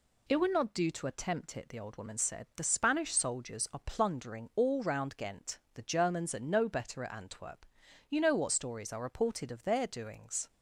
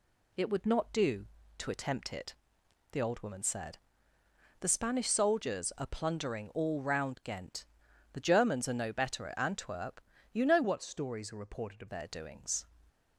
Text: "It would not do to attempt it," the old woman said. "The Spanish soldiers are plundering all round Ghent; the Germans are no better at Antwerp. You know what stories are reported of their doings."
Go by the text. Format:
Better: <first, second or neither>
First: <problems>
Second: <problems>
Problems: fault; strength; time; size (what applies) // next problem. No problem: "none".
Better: first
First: none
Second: changes voice from "what" to "of"; from 10.6 to 11.8 s; 1.2 s long